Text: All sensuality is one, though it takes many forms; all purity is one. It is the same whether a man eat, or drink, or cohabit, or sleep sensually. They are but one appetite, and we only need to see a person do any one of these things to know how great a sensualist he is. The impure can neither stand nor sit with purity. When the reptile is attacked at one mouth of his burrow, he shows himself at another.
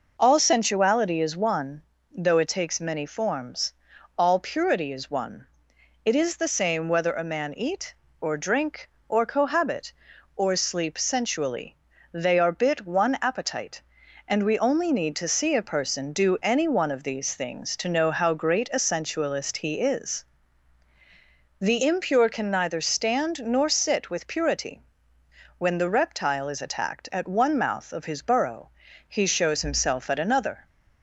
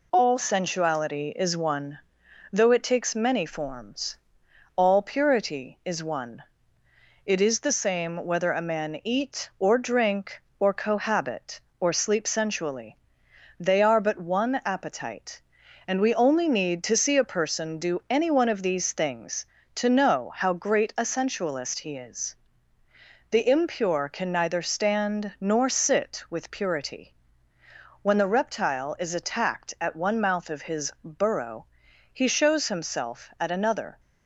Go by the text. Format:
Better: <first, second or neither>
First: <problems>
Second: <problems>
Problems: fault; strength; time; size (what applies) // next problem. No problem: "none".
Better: second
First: says "bit" for "but"; at 12.5 s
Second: none